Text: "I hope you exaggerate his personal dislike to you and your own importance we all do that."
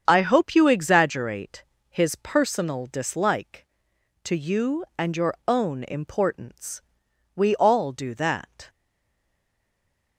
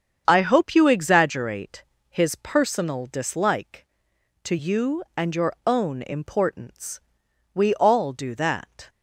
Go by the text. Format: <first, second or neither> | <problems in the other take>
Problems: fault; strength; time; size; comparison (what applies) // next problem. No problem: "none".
second | starts louder than the rest; strong; until 1.0 s; 7.5 dB; strong in the second // pauses between "exaggerate" and "his"; slight; at 1.6 s; 0.26 s long; slight in the second // pauses between "importance" and "we"; noticeable; at 6.8 s; 0.54 s long; noticeable in the second // stays silent after the last word; noticeable; from 8.6 s on; 1.5 s long